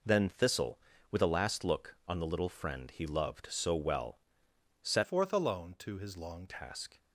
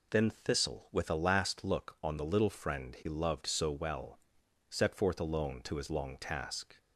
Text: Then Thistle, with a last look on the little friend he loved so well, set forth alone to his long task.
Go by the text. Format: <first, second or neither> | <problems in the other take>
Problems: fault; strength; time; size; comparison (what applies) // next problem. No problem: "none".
second | changes voice from "forth" to "long"; from 5.0 to 6.4 s; 1.4 s long